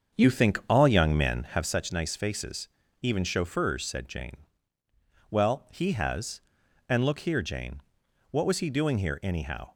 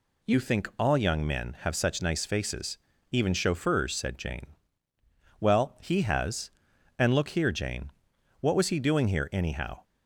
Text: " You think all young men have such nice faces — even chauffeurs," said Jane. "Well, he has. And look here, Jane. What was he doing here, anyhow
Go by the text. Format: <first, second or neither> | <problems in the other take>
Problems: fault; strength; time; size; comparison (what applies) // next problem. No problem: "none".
second | starts louder than the rest; strong; until 1.8 s; 7 dB